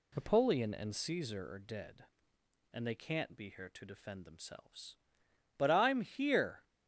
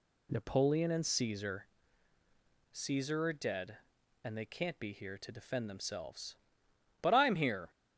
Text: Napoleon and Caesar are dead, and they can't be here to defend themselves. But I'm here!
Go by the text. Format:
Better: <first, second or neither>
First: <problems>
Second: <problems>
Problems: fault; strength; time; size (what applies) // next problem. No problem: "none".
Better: first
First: none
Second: says "Caesar" twice; at 2.7 s